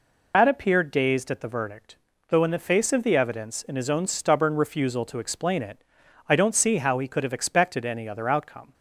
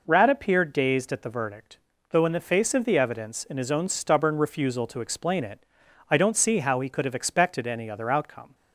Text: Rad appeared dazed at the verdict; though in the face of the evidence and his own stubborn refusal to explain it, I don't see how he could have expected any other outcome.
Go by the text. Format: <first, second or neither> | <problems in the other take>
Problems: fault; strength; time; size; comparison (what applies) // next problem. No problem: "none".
second | loses the start of "Rad"; at 0.3 s; 100 ms